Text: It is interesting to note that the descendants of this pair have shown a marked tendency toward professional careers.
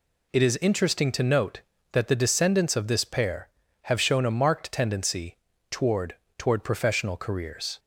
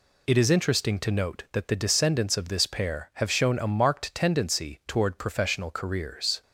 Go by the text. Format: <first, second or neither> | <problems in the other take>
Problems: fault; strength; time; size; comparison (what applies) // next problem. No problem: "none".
second | pauses between "tendency" and "toward"; slight; at 5.3 s; 0.34 s long // says "toward" twice; at 6.3 s